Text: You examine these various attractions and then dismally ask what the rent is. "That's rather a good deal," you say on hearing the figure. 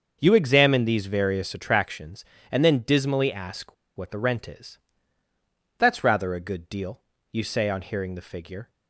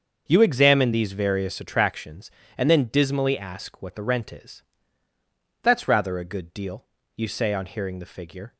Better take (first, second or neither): second